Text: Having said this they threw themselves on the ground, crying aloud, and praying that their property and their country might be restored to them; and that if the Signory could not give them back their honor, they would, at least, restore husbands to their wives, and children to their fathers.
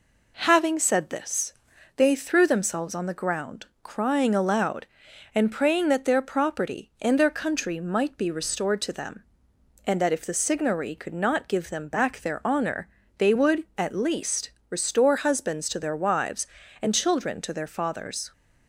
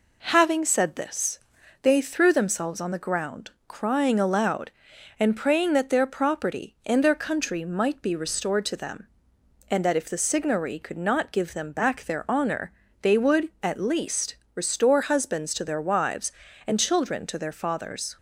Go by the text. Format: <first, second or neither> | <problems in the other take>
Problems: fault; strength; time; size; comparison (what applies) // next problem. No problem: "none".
neither | pauses between "this" and "they"; the same in both